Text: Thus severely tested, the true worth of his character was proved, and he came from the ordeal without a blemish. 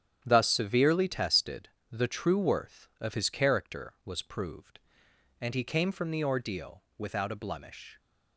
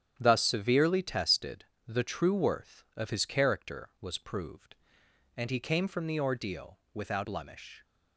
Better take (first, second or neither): first